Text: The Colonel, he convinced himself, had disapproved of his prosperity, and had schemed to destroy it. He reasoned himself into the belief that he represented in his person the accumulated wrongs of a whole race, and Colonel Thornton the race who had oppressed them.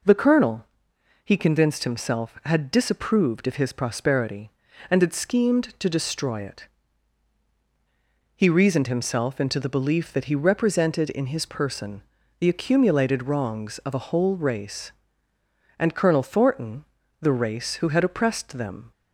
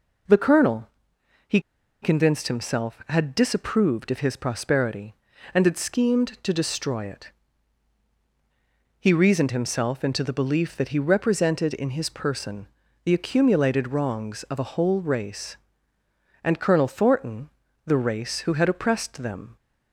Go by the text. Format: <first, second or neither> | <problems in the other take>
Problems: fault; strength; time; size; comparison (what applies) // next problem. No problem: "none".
first | pauses between "he" and "convinced"; at 1.5 s; 0.42 s long // pauses between "person" and "the"; at 12.6 s; 0.38 s long; also in the first // pauses between "Thornton" and "the"; at 17.4 s; 0.38 s long; also in the first